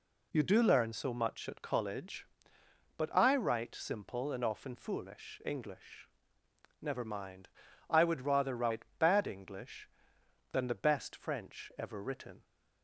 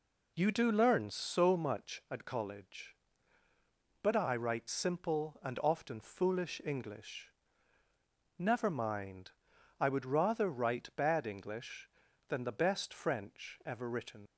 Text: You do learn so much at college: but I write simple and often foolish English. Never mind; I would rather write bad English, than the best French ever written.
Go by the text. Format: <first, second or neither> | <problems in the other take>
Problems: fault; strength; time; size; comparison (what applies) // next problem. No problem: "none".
first | leaves "written" unfinished; at 14.2 s; 75 ms